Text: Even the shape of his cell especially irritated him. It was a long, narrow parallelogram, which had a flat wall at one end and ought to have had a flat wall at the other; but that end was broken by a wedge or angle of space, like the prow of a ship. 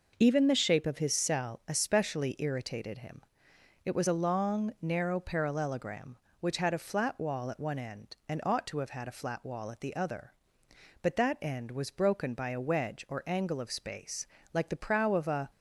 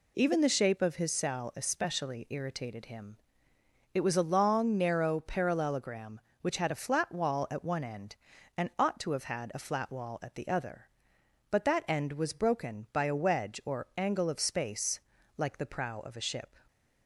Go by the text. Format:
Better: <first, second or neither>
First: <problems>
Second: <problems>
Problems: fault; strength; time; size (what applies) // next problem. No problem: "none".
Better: second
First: stops before "ship"; at 15.4 s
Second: none